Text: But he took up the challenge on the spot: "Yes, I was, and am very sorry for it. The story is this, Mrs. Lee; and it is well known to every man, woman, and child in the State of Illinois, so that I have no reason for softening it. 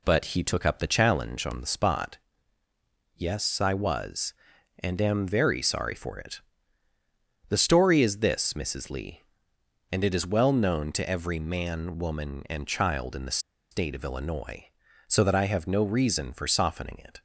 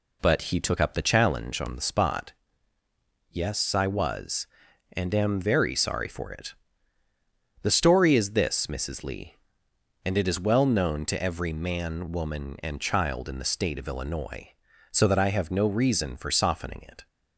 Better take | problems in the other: second | pauses between "the" and "State"; slight; at 13.3 s; 0.32 s long

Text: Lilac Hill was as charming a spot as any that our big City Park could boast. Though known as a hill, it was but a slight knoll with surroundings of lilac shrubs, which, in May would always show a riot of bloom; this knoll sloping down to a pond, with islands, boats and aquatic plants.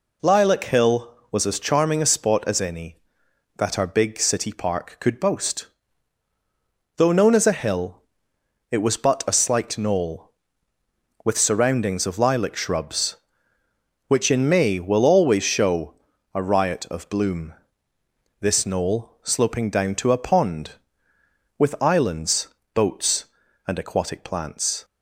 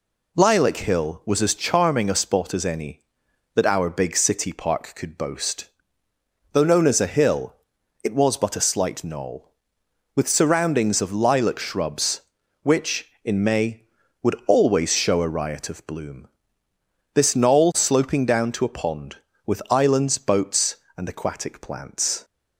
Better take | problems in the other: second | says "will" for "would"; at 14.8 s // pauses between "show" and "a"; at 15.9 s; 0.40 s long

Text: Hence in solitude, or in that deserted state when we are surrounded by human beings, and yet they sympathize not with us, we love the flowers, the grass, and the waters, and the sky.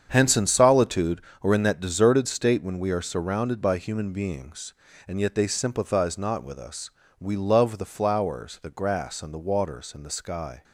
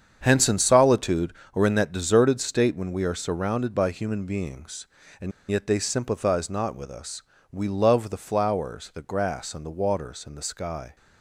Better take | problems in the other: first | starts louder than the rest; strong; until 1.2 s; 7.5 dB; strong in the first // pauses between "and" and "yet"; slight; at 5.3 s; 0.19 s long

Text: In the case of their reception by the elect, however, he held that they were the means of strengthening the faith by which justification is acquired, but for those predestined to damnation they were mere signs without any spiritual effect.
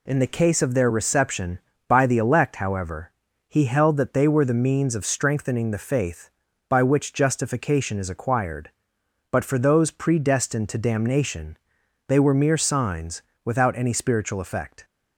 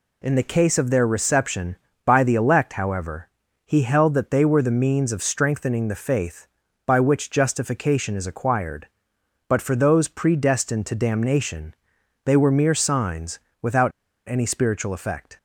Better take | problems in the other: first | pauses between "damnation" and "they"; noticeable; at 11.7 s; 0.50 s long; noticeable in the first // pauses between "signs" and "without"; slight; at 13.4 s; 0.20 s long; slight in the first // pauses between "without" and "any"; slight; at 13.9 s; 0.35 s long

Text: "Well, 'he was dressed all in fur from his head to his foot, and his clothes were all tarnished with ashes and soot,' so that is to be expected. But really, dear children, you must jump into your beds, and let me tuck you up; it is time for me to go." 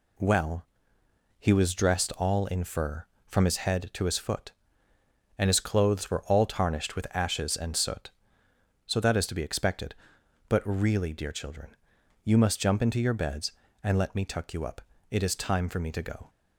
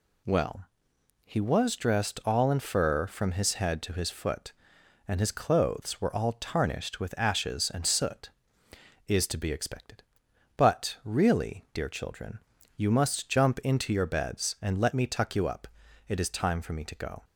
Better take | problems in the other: first | skips "so that"; at 8.6 s

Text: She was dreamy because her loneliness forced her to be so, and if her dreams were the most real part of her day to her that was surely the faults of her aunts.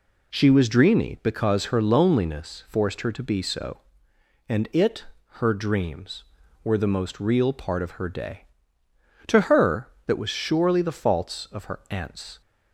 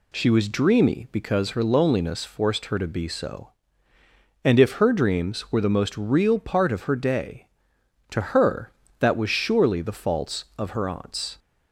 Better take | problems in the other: second | says "it" for "if"; at 4.7 s

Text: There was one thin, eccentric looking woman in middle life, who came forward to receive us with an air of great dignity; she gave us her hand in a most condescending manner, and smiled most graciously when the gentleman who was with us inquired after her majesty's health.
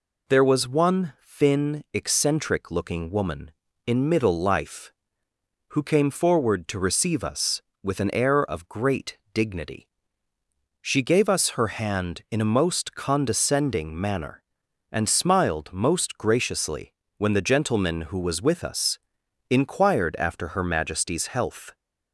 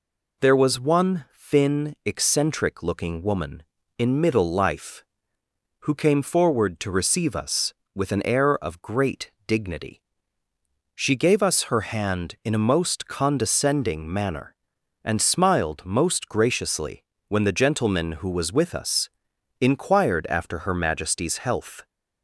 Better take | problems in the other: neither | pauses between "great" and "dignity"; slight; the same in both // pauses between "graciously" and "when"; slight; the same in both // pauses between "us" and "inquired"; noticeable; the same in both

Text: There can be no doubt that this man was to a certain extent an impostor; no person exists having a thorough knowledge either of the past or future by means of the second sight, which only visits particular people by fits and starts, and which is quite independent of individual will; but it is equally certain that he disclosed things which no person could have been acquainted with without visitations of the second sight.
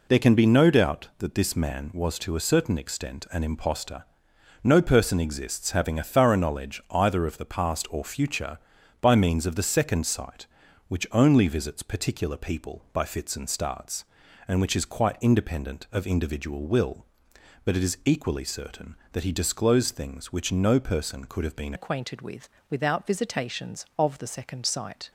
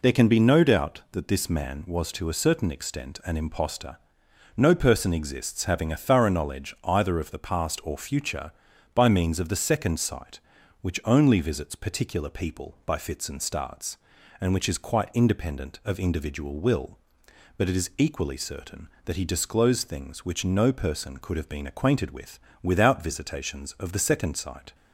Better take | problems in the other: second | changes voice at "acquainted"; from 21.7 s on; 3.4 s long // pauses between "with" and "without"; slight; at 22.4 s; 0.22 s long; slight in the second

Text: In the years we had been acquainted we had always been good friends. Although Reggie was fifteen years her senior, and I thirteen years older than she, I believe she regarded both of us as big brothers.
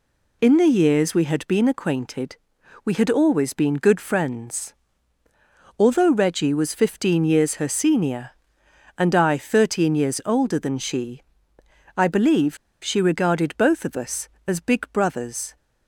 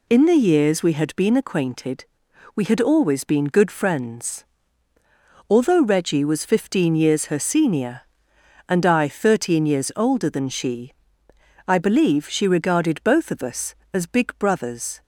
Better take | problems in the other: second | pauses between "acquainted" and "we"; noticeable; at 2.3 s; 0.48 s long; noticeable in the second // pauses between "believe" and "she"; slight; at 12.5 s; 0.26 s long

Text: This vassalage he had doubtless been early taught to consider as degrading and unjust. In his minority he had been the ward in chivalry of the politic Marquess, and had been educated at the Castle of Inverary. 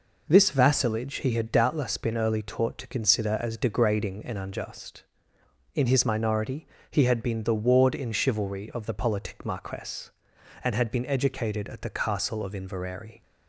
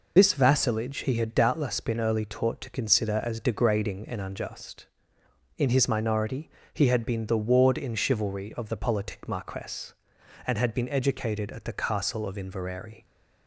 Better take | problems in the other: first | loses the start of "This"; at 0.1 s; 55 ms // pauses between "minority" and "he"; slight; at 6.4 s; 0.24 s long; slight in the first

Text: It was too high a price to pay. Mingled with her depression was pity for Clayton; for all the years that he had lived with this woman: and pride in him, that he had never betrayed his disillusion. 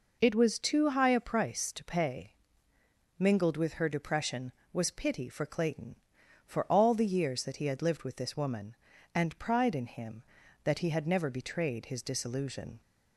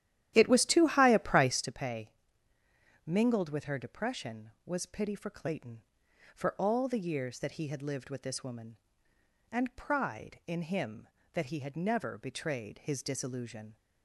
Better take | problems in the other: first | starts louder than the rest; strong; until 1.8 s; 11.5 dB

